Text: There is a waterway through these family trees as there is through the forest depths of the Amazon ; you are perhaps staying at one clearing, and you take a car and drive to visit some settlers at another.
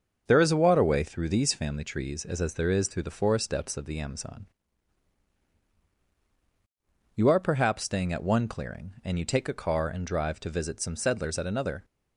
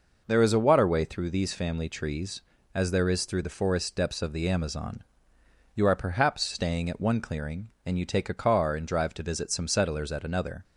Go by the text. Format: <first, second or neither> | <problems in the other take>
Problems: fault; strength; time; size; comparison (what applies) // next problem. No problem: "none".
second | starts louder than the rest; until 1.2 s; 6.5 dB // says "as" twice; at 2.4 s